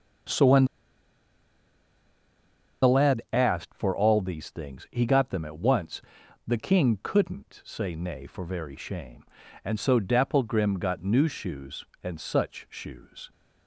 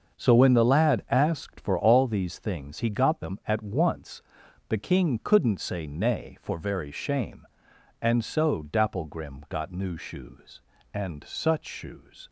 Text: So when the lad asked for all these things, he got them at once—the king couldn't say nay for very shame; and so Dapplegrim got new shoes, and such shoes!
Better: second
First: starts louder than the rest; until 3.5 s; 7 dB // pauses between "when" and "the"; strong; at 0.6 s; 2.1 s long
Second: starts louder than the rest; until 1.2 s; 6.5 dB

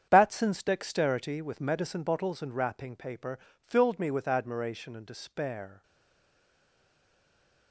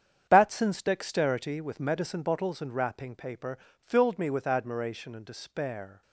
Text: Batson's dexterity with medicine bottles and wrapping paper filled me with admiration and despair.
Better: second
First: starts louder than the rest; strong; until 1.1 s; 8.5 dB // pauses between "paper" and "filled"; slight; at 3.3 s; 0.22 s long // stays silent after the last word; noticeable; from 5.8 s on; 1.9 s long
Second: starts louder than the rest; strong; until 1.3 s; 8.5 dB // pauses between "paper" and "filled"; slight; at 3.5 s; 0.22 s long

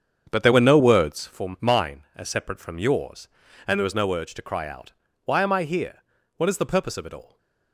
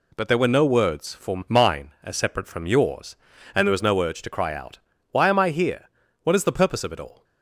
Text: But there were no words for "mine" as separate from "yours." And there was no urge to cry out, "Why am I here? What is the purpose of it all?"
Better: second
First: starts louder than the rest; strong; until 1.4 s; 7.5 dB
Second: none

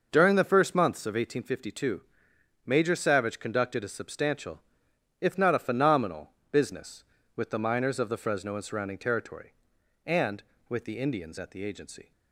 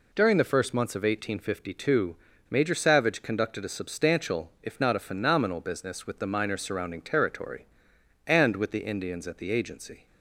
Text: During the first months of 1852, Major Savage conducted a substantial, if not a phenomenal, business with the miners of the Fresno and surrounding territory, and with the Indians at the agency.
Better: first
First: none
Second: skips "of the Fresno and"; at 6.6 s

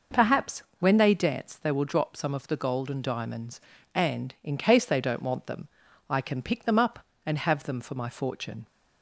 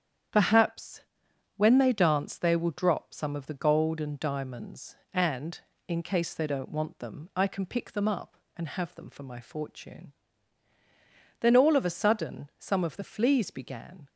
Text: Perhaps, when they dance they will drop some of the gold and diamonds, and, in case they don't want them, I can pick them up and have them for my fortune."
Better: first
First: none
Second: starts louder than the rest; strong; until 1.8 s; 9 dB // goes on to say "Then all of a sudden some of the fleas began"; strong; from 11.3 s on; 2.6 s long

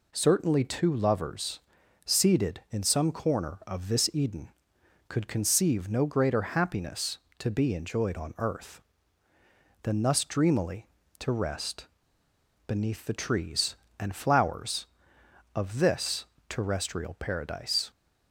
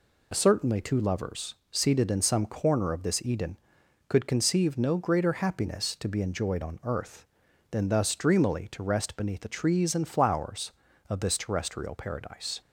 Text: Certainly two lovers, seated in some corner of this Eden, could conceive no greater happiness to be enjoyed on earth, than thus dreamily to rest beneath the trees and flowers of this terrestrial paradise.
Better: second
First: pauses between "rest" and "beneath"; noticeable; at 11.8 s; 0.79 s long // pauses between "this" and "terrestrial"; slight; at 16.2 s; 0.24 s long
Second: none

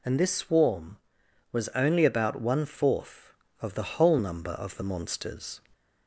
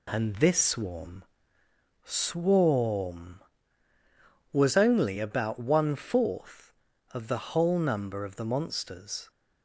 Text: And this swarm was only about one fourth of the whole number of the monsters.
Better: first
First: none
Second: says "swarm" twice; at 2.0 s

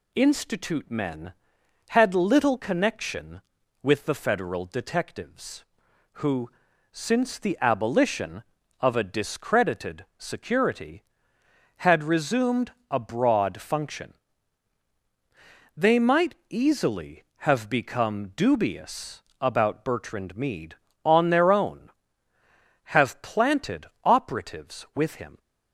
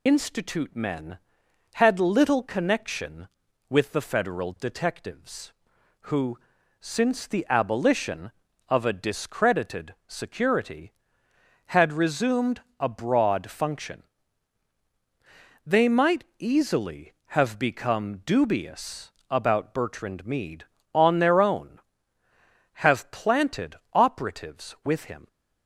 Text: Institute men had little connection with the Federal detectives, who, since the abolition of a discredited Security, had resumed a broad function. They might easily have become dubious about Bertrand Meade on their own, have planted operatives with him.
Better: first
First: pauses between "resumed" and "a"; slight; at 12.7 s; 0.18 s long // pauses between "might" and "easily"; slight; at 16.3 s; 0.16 s long // pauses between "dubious" and "about"; slight; at 19.2 s; 0.18 s long // pauses between "planted" and "operatives"; slight; at 23.8 s; 0.18 s long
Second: loses the start of "Institute"; at 0.0 s; 60 ms // pauses between "resumed" and "a"; slight; at 12.6 s; 0.18 s long // pauses between "might" and "easily"; slight; at 16.2 s; 0.16 s long // pauses between "dubious" and "about"; slight; at 19.1 s; 0.18 s long // pauses between "planted" and "operatives"; slight; at 23.7 s; 0.18 s long

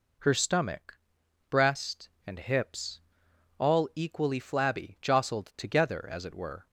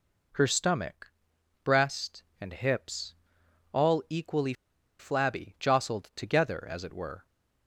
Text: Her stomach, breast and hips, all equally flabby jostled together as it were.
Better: first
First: none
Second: pauses between "equally" and "flabby"; noticeable; at 4.5 s; 0.46 s long

